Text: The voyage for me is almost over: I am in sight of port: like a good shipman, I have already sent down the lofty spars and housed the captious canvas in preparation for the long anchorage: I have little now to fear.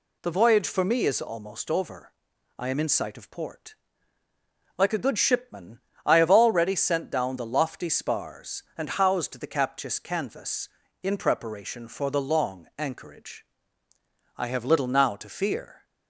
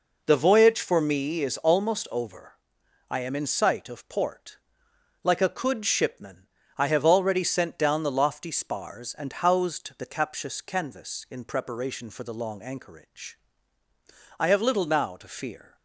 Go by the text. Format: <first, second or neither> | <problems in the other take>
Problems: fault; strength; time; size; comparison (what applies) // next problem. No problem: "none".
first | says "could" for "good"; at 5.4 s